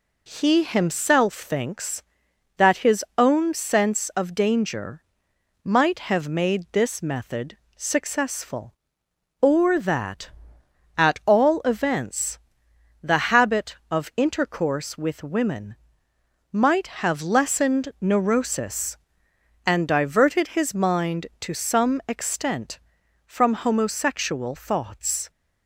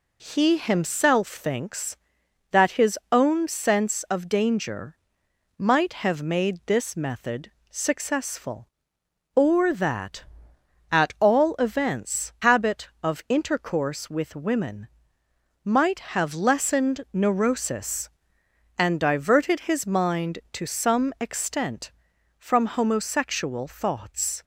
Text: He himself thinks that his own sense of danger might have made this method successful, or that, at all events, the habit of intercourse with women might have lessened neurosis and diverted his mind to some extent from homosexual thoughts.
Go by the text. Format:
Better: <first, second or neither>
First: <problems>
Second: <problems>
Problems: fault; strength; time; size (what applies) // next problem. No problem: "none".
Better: first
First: pauses between "danger" and "might"; noticeable; at 5.0 s; 0.62 s long // pauses between "method" and "successful"; slight; at 7.5 s; 0.22 s long // pauses between "women" and "might"; noticeable; at 15.7 s; 0.74 s long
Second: pauses between "danger" and "might"; noticeable; at 4.9 s; 0.62 s long // pauses between "method" and "successful"; slight; at 7.4 s; 0.22 s long // skips "the"; at 12.3 s // pauses between "women" and "might"; noticeable; at 14.8 s; 0.74 s long